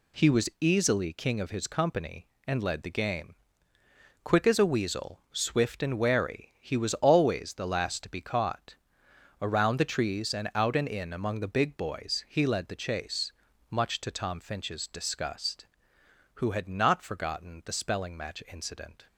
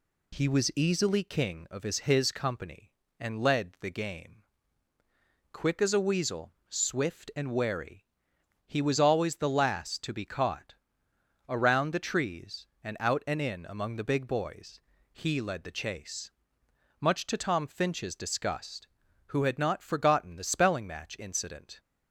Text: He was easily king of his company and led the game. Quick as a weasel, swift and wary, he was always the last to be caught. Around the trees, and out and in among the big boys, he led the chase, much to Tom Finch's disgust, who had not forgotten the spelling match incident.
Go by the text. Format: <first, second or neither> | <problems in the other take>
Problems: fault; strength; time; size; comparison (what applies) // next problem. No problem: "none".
first | says "his" twice; at 2.0 s